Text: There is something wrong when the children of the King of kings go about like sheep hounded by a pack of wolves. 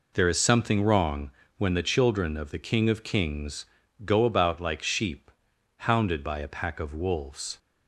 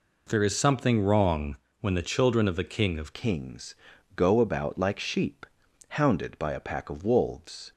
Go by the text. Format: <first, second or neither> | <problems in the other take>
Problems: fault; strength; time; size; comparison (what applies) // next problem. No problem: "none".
first | pauses between "wrong" and "when"; slight; at 1.5 s; 0.24 s long; slight in the first // changes voice at "kings"; from 3.1 s on; 4.6 s long // pauses between "kings" and "go"; at 3.7 s; 0.42 s long; also in the first // pauses between "sheep" and "hounded"; at 5.4 s; 0.44 s long; noticeable in the first